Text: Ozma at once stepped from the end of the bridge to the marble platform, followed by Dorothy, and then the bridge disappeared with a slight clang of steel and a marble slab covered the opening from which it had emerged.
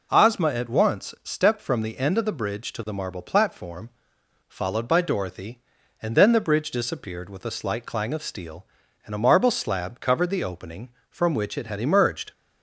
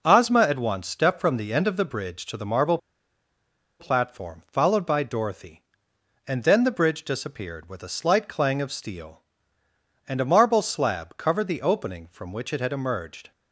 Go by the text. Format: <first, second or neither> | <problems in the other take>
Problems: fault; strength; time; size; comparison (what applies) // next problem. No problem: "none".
first | pauses between "marble" and "platform"; at 2.7 s; 1.0 s long